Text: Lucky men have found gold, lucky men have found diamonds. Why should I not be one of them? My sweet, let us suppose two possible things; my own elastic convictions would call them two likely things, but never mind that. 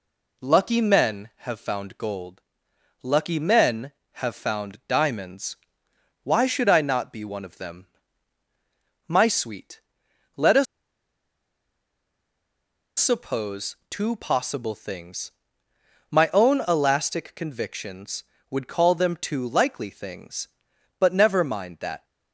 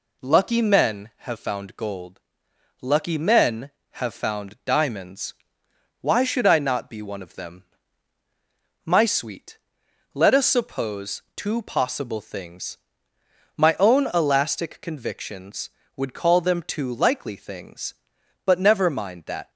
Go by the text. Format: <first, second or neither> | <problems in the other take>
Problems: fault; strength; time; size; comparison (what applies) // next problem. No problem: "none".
second | pauses between "us" and "suppose"; strong; at 10.6 s; 2.3 s long // pauses between "suppose" and "two"; slight; at 13.7 s; 0.16 s long; slight in the second